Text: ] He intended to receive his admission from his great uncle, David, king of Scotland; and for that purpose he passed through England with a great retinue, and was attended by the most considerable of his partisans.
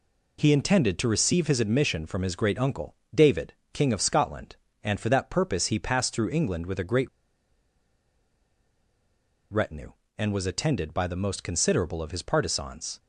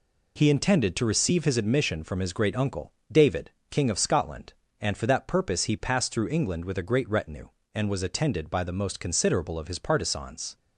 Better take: second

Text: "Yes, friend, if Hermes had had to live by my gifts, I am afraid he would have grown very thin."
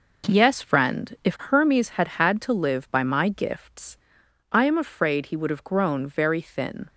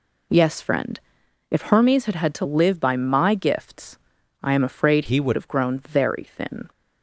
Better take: first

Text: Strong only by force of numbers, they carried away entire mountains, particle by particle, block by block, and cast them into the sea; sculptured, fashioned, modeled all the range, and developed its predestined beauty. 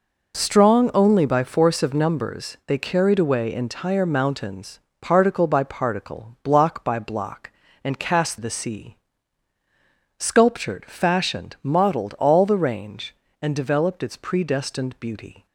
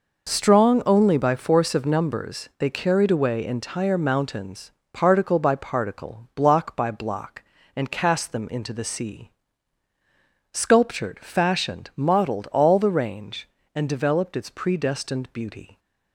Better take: second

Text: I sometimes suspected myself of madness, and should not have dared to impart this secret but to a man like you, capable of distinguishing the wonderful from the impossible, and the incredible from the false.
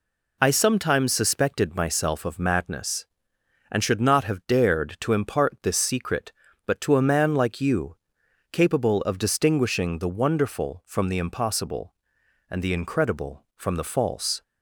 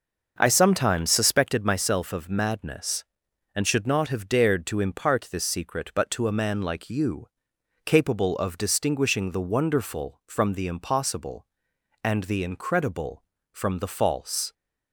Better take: first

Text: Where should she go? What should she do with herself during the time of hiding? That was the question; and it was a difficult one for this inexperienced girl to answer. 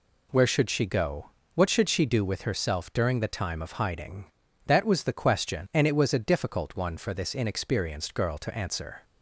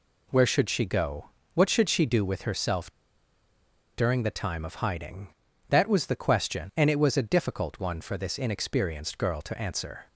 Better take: first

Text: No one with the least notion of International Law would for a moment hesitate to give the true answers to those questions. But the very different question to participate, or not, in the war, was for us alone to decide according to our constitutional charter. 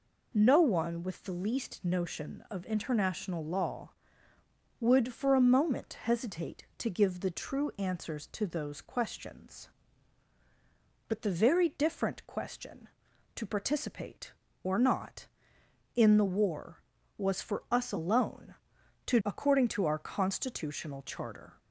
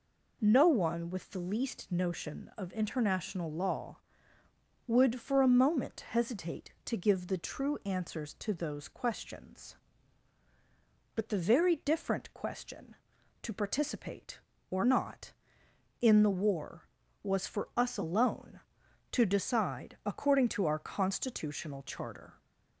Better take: second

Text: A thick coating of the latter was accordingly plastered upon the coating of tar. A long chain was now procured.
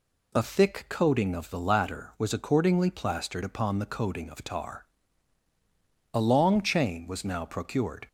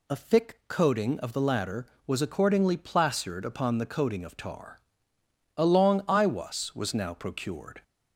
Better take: first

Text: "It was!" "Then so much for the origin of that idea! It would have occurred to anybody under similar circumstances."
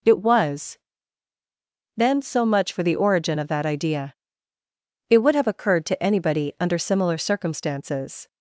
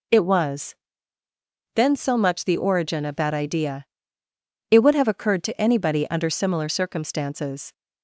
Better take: first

